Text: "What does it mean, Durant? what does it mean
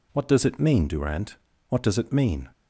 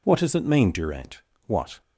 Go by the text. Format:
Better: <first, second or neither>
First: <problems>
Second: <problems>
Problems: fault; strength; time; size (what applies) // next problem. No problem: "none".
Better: first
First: none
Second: stops before "does it mean"; at 1.8 s